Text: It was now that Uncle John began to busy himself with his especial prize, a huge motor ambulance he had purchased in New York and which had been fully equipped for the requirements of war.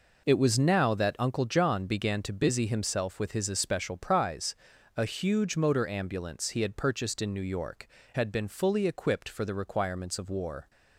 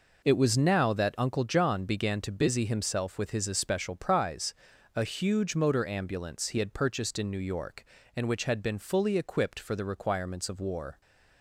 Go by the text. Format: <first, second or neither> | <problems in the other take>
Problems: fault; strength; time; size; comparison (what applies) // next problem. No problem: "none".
second | skips "and which"; at 8.0 s